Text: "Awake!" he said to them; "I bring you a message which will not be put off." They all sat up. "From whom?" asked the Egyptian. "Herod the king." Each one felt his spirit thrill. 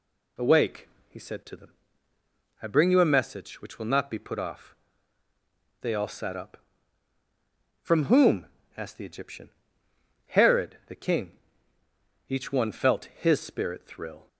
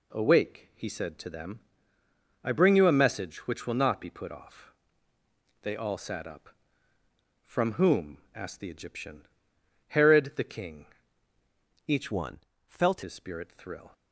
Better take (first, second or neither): first